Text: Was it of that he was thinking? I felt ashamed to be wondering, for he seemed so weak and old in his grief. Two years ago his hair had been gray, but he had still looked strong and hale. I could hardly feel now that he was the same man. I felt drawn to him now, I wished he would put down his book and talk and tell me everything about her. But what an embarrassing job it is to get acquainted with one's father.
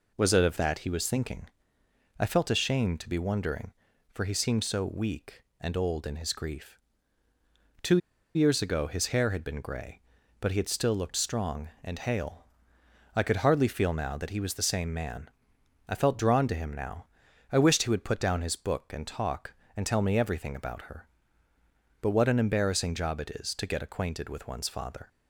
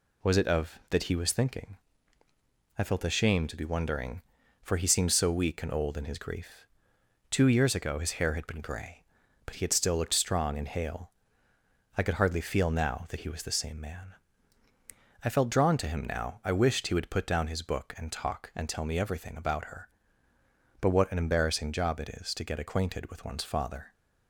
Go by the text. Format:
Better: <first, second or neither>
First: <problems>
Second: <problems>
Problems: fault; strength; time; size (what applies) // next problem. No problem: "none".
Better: second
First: pauses between "Two" and "years"; at 7.9 s; 0.37 s long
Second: none